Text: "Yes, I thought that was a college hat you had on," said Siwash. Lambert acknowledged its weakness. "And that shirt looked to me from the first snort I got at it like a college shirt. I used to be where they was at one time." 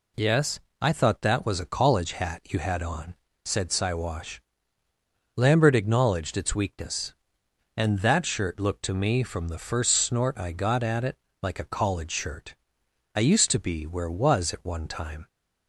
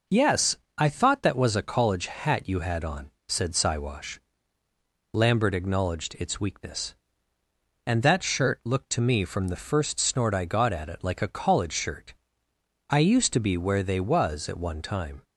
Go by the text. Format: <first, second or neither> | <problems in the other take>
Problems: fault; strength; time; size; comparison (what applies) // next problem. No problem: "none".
second | pauses between "it" and "like"; slight; at 11.1 s; 0.26 s long // skips "they"; at 14.0 s